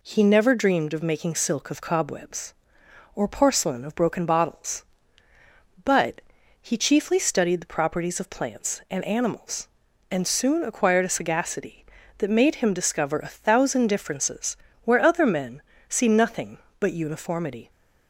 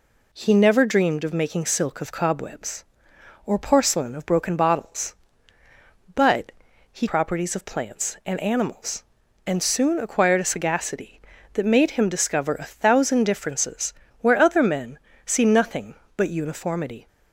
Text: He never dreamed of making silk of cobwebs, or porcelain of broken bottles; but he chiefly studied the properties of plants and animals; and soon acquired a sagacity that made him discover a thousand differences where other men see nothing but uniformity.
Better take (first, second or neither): first